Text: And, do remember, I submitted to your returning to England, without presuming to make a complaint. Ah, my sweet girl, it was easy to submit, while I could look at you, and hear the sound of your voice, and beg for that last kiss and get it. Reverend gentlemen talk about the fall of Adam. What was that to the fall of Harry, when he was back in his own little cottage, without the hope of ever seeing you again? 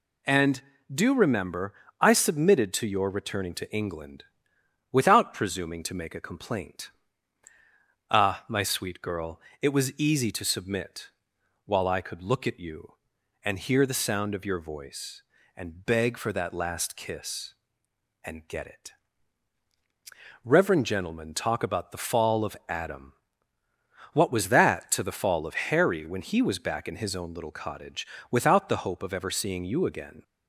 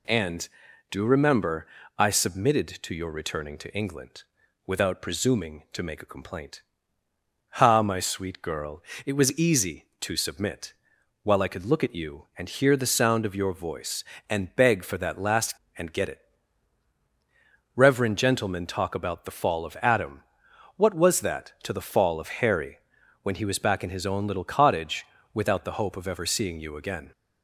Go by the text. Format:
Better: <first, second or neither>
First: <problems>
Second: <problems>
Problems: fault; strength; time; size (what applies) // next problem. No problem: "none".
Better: first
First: none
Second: skips "kiss"; at 15.6 s